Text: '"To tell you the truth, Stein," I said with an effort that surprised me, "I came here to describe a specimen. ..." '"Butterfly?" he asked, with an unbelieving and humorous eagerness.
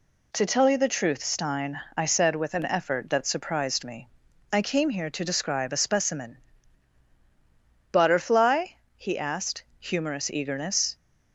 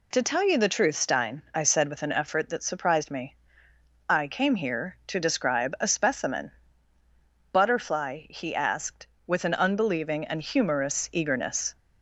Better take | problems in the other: second | skips "with an unbelieving and"; at 9.7 s

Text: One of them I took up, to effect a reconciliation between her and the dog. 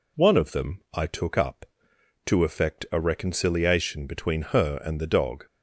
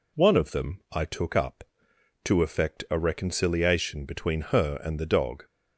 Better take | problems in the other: neither | none

